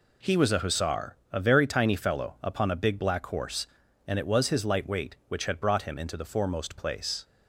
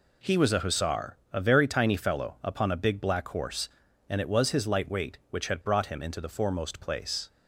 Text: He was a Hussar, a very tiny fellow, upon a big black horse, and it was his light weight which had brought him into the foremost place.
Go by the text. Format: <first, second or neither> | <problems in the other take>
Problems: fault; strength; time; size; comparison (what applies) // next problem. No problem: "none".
neither | none